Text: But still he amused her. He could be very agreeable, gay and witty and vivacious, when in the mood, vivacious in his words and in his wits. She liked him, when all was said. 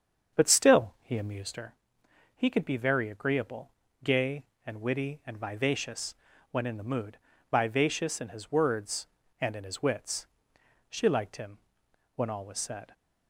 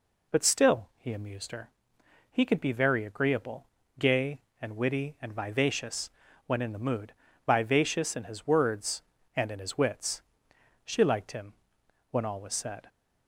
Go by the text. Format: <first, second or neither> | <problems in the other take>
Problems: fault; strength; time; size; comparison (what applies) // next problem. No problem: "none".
second | starts louder than the rest; strong; until 1.7 s; 7.5 dB